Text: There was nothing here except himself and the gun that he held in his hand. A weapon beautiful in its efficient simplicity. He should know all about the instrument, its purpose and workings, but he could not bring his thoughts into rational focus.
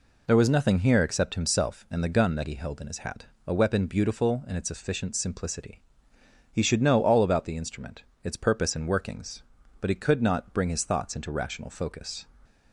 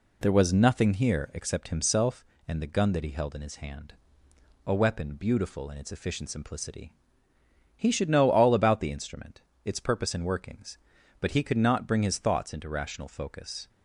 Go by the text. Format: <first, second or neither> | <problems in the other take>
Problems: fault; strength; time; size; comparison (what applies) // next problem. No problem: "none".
second | says "hat" for "hand"; at 2.9 s